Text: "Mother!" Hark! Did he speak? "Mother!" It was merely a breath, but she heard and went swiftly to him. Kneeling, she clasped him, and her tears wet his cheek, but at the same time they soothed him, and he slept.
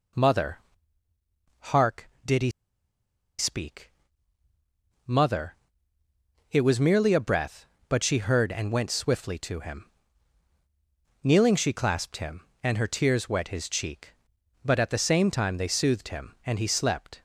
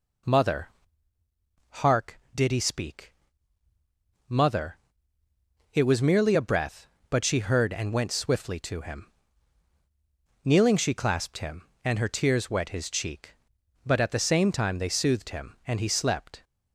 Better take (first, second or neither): second